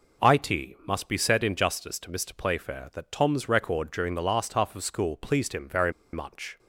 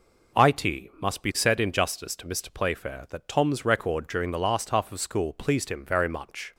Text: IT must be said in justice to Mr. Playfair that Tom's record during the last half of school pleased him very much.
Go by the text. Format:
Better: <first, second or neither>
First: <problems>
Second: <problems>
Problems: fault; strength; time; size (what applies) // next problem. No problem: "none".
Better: second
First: pauses between "very" and "much"; slight; at 5.9 s; 0.21 s long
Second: none